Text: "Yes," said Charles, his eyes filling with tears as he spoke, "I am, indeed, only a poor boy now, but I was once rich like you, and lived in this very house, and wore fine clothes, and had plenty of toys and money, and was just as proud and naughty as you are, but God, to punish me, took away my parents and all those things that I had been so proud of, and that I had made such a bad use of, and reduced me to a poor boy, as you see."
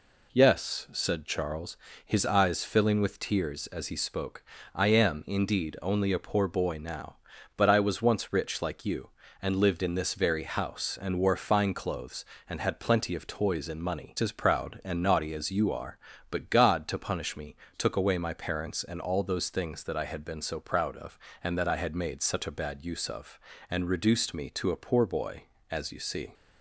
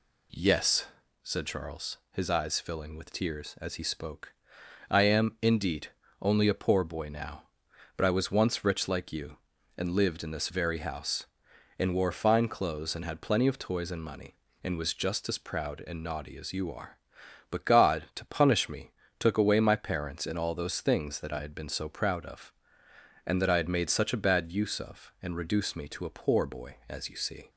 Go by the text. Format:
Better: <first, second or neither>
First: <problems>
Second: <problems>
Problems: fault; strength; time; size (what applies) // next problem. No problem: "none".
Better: second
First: skips "and was just"; at 14.1 s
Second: none